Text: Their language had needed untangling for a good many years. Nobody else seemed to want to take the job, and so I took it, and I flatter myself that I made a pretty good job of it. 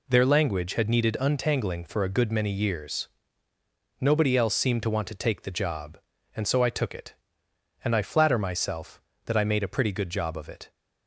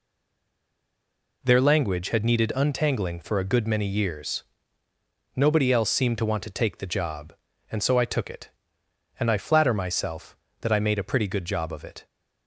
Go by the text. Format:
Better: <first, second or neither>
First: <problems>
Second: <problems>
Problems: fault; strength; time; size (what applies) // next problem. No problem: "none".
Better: first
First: none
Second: stays silent before the first word; noticeable; until 1.4 s; 1.4 s long